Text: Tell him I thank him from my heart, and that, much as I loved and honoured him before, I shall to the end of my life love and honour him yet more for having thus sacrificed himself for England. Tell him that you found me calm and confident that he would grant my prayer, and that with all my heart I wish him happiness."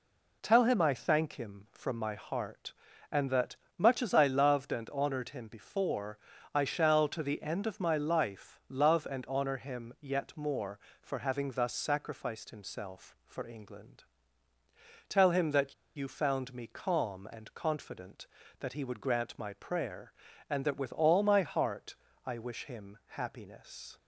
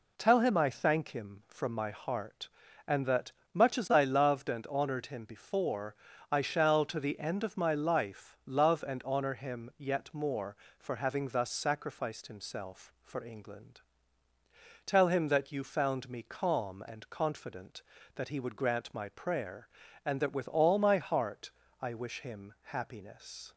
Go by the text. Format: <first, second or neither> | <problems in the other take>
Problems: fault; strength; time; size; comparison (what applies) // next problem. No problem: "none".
second | pauses between "that" and "you"; slight; at 15.7 s; 0.21 s long // pauses between "heart" and "I"; slight; at 21.9 s; 0.28 s long; slight in the second